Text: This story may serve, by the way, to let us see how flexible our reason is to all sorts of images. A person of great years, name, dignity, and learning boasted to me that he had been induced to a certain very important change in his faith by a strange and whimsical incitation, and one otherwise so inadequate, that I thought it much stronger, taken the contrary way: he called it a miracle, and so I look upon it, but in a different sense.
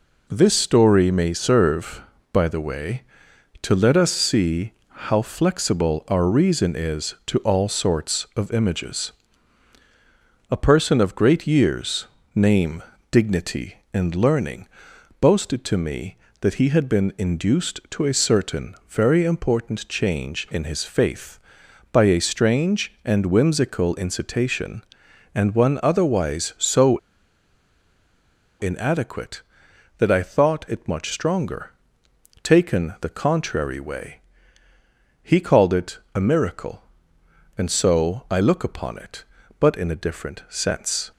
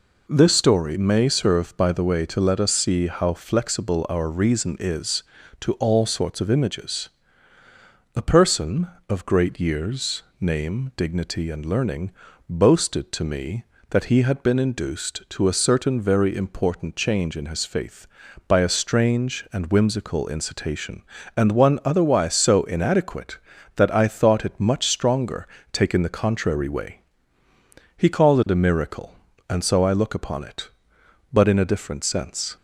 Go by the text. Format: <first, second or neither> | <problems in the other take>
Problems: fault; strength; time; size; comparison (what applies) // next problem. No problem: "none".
second | pauses between "see" and "how"; slight; at 4.7 s; 0.34 s long // pauses between "learning" and "boasted"; noticeable; at 14.6 s; 0.54 s long; also in the second // pauses between "so" and "inadequate"; strong; at 26.9 s; 1.6 s long // pauses between "it" and "a"; slight; at 35.9 s; 0.16 s long